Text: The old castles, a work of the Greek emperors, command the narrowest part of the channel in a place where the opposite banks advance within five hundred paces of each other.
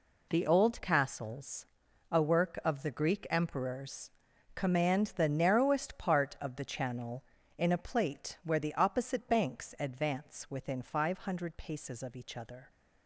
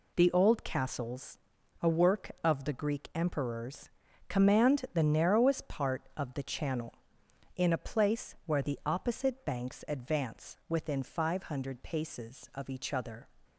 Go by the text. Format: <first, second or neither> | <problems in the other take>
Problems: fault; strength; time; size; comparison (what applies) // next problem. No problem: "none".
second | says "plate" for "place"; at 7.7 s